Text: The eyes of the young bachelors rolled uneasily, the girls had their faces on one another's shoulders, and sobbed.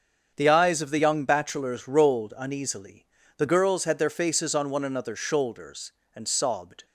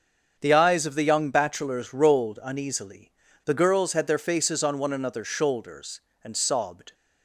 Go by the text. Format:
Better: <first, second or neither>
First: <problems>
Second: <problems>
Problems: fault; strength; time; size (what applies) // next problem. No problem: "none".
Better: neither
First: starts louder than the rest; strong; until 1.3 s; 7.5 dB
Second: starts louder than the rest; strong; until 1.4 s; 7 dB